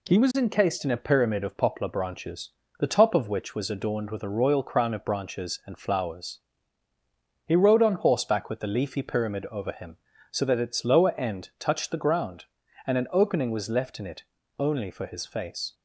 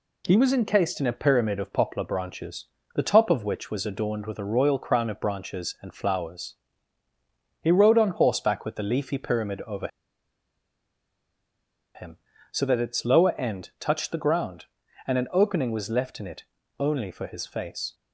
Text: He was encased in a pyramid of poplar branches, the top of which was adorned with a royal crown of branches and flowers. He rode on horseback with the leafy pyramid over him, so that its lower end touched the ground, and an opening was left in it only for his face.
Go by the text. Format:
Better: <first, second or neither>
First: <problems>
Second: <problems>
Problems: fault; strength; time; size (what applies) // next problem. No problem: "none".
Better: first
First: pauses between "it" and "only"; slight; at 14.2 s; 0.34 s long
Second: pauses between "over" and "him"; strong; at 9.8 s; 2.0 s long // pauses between "it" and "only"; slight; at 16.4 s; 0.34 s long